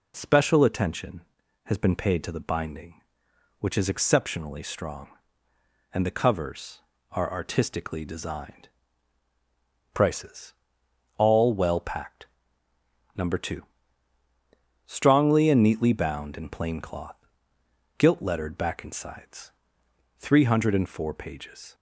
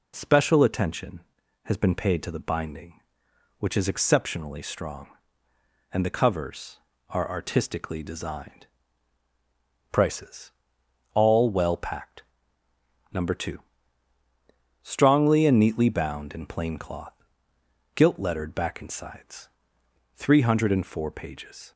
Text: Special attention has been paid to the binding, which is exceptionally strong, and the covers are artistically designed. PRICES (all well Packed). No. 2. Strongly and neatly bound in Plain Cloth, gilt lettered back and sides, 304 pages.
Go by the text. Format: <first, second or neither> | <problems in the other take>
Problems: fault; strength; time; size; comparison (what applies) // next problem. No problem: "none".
neither | none